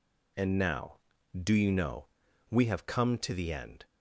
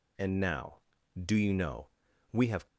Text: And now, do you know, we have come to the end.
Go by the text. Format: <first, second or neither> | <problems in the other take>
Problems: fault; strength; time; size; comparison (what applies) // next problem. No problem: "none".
first | stops before "come to the end"; at 2.6 s